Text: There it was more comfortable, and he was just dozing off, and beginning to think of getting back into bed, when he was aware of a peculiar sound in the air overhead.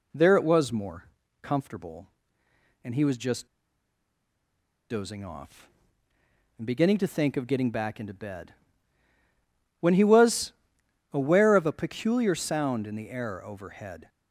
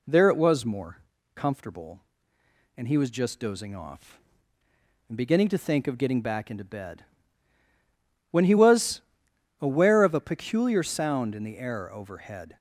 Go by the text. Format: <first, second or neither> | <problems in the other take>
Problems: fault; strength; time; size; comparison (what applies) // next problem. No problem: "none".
second | pauses between "more" and "comfortable"; slight; at 1.0 s; 0.36 s long; slight in the second // pauses between "just" and "dozing"; strong; at 3.4 s; 1.4 s long // pauses between "was" and "aware"; noticeable; at 10.5 s; 0.60 s long; noticeable in the second